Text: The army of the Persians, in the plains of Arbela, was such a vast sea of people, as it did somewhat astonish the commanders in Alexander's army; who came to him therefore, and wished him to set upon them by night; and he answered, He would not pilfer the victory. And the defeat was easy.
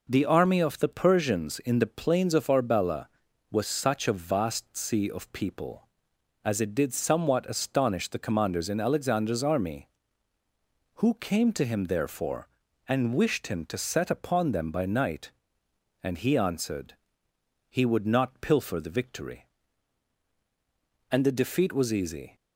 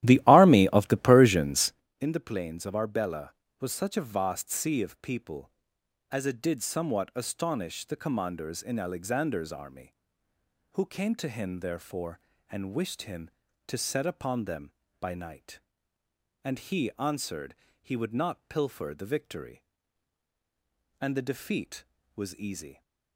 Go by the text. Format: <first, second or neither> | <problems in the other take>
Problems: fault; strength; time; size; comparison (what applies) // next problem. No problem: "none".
first | starts louder than the rest; strong; until 1.9 s; 14 dB